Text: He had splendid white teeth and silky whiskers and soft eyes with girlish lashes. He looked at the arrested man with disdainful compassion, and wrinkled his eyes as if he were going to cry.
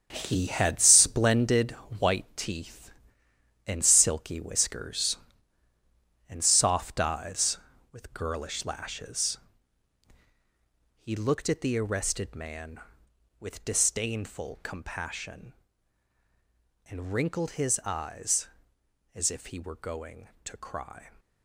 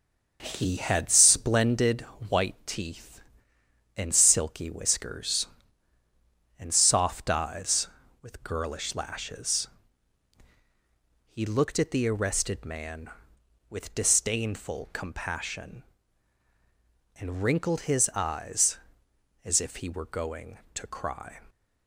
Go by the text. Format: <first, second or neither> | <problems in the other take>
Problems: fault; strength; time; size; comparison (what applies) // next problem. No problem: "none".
second | gets quieter; strong; throughout; 10.5 dB // starts louder than the rest; strong; until 1.1 s; 7.5 dB; noticeable in the second // pauses between "splendid" and "white"; slight; at 1.7 s; 0.28 s long; slight in the second